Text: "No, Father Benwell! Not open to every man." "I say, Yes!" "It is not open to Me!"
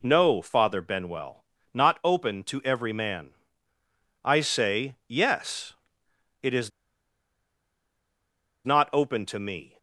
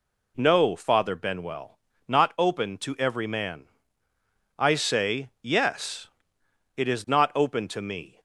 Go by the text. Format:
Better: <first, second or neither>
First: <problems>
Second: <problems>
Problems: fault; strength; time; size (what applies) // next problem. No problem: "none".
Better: second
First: pauses between "is" and "not"; strong; at 6.7 s; 1.9 s long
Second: none